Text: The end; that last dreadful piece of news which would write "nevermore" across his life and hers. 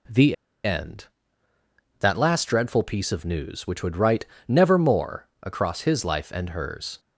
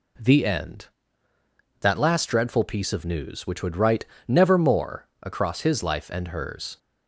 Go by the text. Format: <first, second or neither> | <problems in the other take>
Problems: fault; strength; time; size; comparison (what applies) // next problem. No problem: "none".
second | pauses between "The" and "end"; slight; at 0.3 s; 0.30 s long // pauses between "write" and "nevermore"; slight; at 4.2 s; 0.24 s long; slight in the second